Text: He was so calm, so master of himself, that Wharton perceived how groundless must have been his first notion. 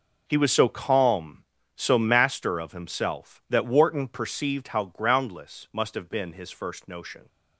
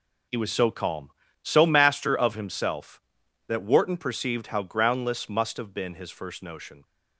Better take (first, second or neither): neither